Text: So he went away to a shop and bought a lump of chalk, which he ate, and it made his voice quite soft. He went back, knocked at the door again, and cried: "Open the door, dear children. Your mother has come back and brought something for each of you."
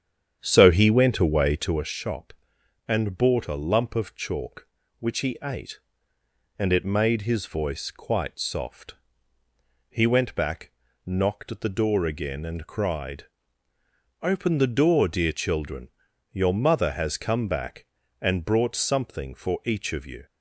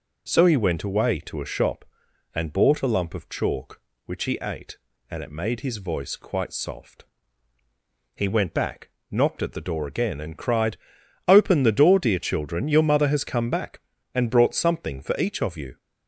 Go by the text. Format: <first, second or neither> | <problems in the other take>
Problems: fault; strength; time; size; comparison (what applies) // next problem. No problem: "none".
second | starts louder than the rest; strong; until 1.8 s; 8.5 dB